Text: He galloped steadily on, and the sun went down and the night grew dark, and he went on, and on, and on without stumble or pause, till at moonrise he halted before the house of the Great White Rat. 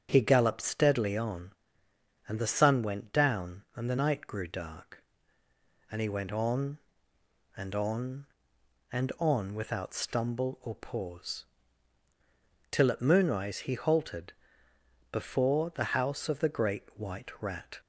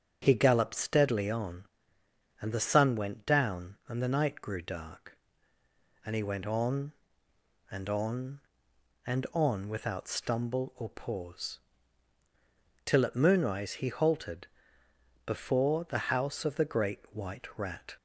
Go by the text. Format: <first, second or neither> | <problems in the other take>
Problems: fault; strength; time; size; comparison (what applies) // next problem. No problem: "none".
neither | starts louder than the rest; strong; the same in both // pauses between "halted" and "before"; noticeable; the same in both